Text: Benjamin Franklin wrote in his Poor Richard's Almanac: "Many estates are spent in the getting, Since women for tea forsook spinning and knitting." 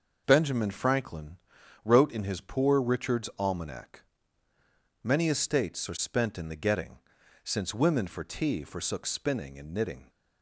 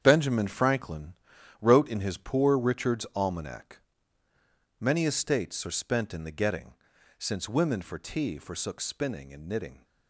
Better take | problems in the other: first | gets quieter; strong; throughout; 10 dB // pauses between "Franklin" and "wrote"; noticeable; at 1.1 s; 0.48 s long; noticeable in the first

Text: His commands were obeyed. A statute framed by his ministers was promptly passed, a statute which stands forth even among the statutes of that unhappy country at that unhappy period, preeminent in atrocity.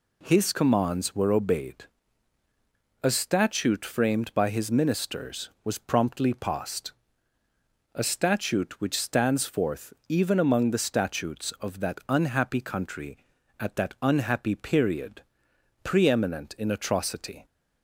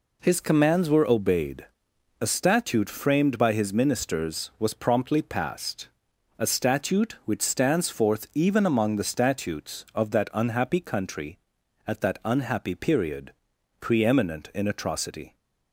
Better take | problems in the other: neither | none

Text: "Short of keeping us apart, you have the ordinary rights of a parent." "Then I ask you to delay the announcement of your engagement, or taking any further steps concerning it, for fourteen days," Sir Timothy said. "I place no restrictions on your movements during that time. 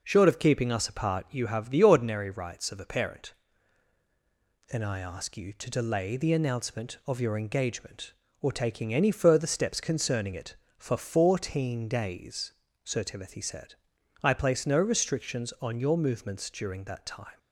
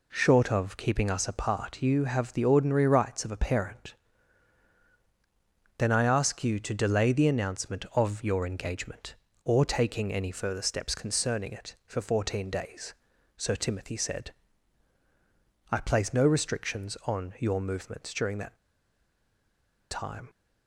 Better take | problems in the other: first | pauses between "that" and "time"; strong; at 18.5 s; 1.3 s long

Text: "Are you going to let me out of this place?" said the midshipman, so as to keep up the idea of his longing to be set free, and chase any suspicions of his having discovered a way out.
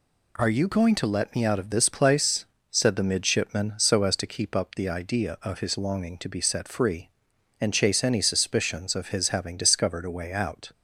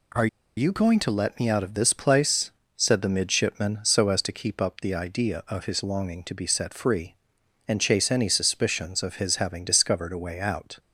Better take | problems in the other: first | pauses between "Are" and "you"; slight; at 0.2 s; 0.30 s long

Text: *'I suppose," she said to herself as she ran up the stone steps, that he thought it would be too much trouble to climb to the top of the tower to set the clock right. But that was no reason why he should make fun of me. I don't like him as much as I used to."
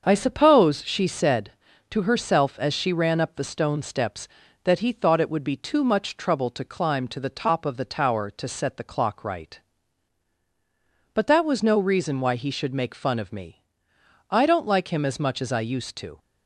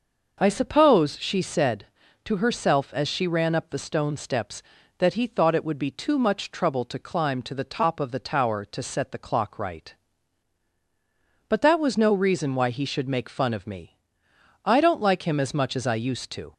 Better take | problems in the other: second | gets quieter; noticeable; throughout; 5 dB

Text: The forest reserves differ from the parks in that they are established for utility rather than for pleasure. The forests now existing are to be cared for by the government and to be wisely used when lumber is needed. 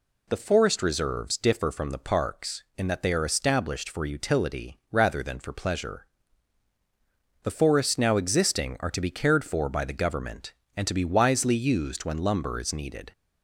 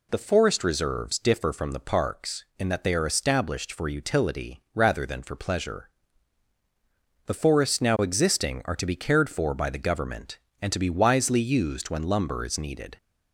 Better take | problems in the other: neither | none

